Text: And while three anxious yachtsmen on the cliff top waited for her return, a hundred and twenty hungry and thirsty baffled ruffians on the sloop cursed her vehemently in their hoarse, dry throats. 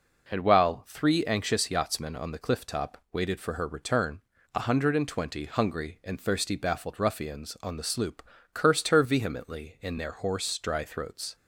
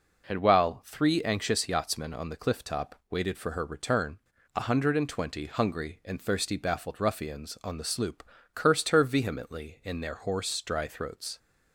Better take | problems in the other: neither | pauses between "top" and "waited"; slight; the same in both // pauses between "sloop" and "cursed"; slight; the same in both

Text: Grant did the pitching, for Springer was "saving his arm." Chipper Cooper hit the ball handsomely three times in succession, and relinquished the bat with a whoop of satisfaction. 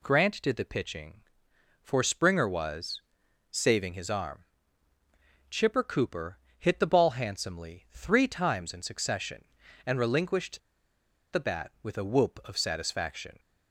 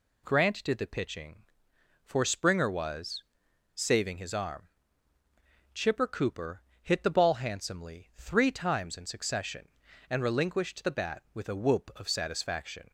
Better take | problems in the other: second | pauses between "was" and "saving"; noticeable; at 3.0 s; 0.52 s long; noticeable in the second // pauses between "Cooper" and "hit"; slight; at 6.3 s; 0.20 s long; slight in the second // pauses between "relinquished" and "the"; noticeable; at 10.5 s; 0.73 s long

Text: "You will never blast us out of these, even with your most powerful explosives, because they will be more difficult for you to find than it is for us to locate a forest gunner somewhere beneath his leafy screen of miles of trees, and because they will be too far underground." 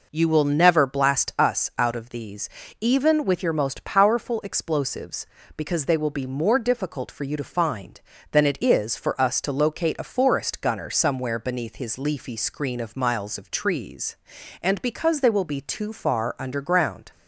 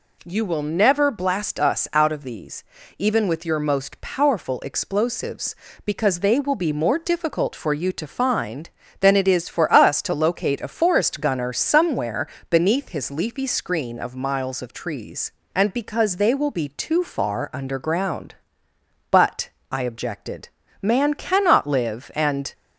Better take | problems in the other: first | pauses between "somewhere" and "beneath"; slight; at 12.2 s; 0.24 s long // goes on to say "But I objected man cannot live and"; strong; from 19.1 s on; 3.4 s long

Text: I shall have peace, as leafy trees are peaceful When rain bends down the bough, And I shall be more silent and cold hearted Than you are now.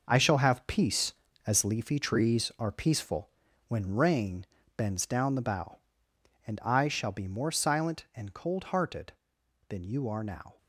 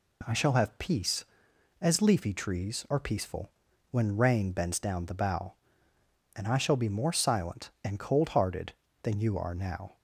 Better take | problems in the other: second | gets quieter; strong; throughout; 8.5 dB // pauses between "peaceful" and "When"; at 3.2 s; 0.38 s long; also in the second // pauses between "rain" and "bends"; slight; at 4.4 s; 0.30 s long

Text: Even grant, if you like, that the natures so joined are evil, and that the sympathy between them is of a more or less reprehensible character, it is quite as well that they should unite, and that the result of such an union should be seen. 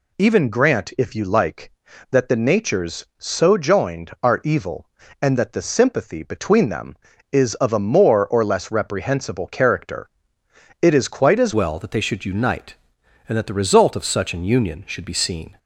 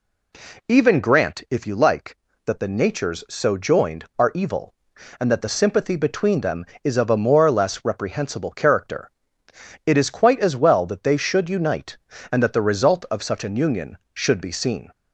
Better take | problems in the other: second | changes voice at "well"; from 11.5 s on; 4.0 s long

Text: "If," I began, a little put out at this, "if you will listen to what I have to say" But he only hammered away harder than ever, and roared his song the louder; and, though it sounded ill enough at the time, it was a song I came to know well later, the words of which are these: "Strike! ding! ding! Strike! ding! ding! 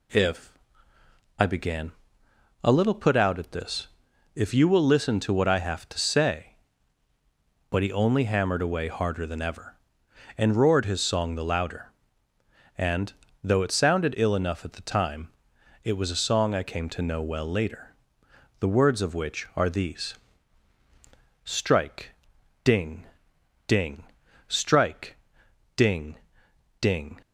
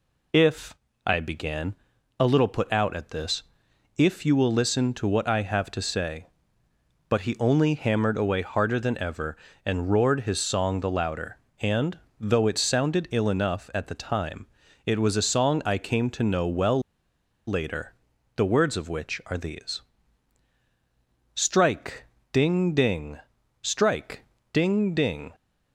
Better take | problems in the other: first | pauses between "well" and "later"; noticeable; at 16.7 s; 0.67 s long

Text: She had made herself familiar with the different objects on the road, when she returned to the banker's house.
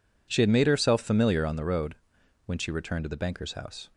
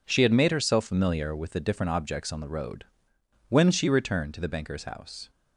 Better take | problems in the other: second | skips "with the different objects"; at 1.4 s

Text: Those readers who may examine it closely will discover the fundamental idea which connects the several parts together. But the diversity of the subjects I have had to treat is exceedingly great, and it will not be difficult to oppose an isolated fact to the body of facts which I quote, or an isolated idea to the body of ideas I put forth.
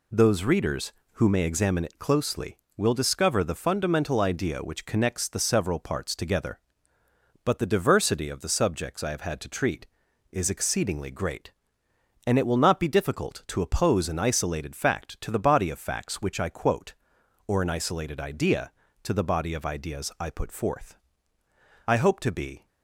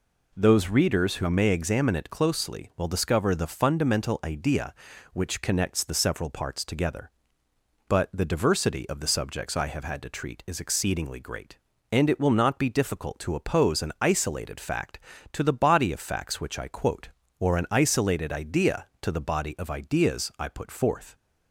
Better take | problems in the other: second | goes on to say "I hope to be"; noticeable; from 21.8 s on; 0.80 s long

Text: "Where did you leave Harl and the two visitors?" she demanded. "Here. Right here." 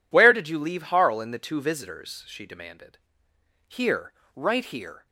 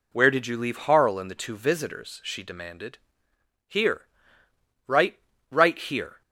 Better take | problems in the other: first | says "Right" twice; at 5.4 s

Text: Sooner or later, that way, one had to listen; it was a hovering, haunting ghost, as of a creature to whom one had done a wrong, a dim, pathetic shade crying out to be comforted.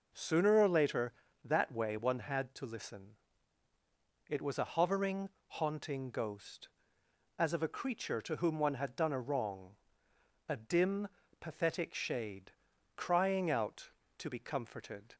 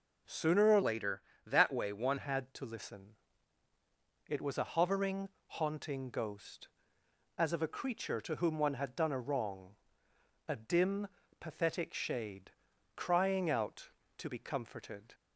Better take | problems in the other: first | changes voice from "later" to "one"; from 0.8 to 2.1 s; 1.3 s long // pauses between "shade" and "crying"; noticeable; at 12.4 s; 0.46 s long; noticeable in the first

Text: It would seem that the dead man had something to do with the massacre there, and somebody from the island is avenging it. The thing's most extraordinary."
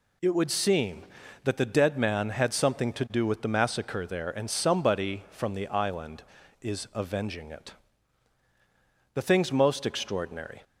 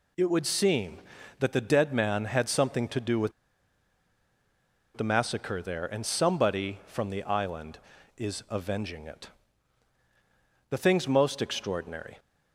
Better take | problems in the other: first | pauses between "with" and "the"; strong; at 3.3 s; 1.6 s long

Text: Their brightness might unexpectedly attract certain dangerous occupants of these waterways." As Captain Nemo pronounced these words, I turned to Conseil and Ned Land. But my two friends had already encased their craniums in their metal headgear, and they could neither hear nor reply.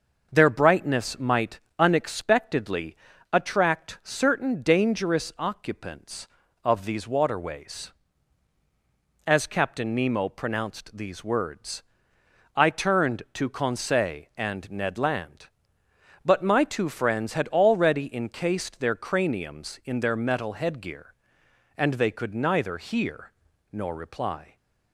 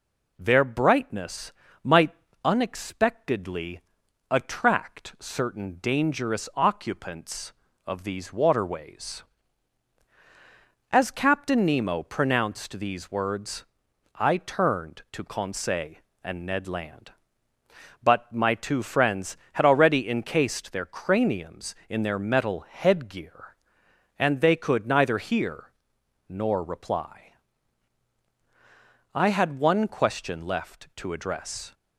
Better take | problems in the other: first | pauses between "brightness" and "might"; slight; at 1.5 s; 0.32 s long // pauses between "might" and "unexpectedly"; slight; at 2.1 s; 0.30 s long; slight in the first // pauses between "unexpectedly" and "attract"; noticeable; at 3.7 s; 0.50 s long; slight in the first // pauses between "hear" and "nor"; noticeable; at 25.7 s; 0.56 s long; also in the first // goes on to say "I had one question left to address"; strong; from 29.1 s on; 2.5 s long

